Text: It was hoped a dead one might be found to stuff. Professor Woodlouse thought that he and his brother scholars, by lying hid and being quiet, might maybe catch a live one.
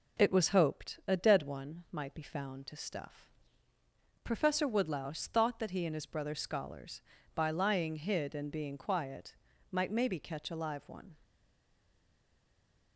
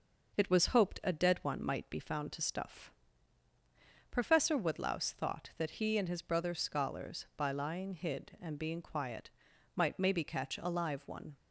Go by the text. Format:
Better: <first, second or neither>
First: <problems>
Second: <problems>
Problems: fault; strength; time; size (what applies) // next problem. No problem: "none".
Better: second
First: stays silent after the last word; noticeable; from 11.2 s on; 1.7 s long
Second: none